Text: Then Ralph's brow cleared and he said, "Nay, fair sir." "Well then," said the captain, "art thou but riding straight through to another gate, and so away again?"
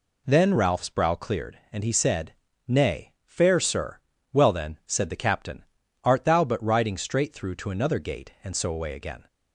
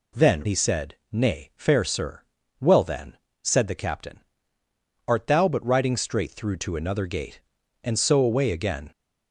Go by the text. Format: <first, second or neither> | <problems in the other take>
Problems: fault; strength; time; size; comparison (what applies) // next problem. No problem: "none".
first | skips "Ralph's brow cleared and"; at 0.4 s